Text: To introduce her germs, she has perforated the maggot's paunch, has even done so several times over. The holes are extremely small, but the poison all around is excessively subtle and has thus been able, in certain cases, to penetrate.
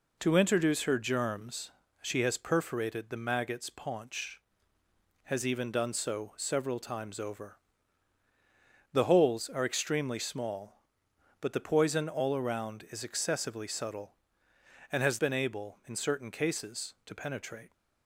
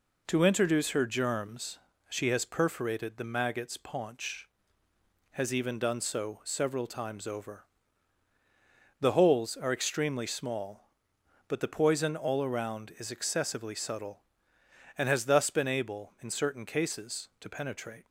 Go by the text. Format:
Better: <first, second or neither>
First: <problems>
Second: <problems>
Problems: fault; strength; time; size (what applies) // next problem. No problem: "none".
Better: second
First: skips "thus"; at 15.1 s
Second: none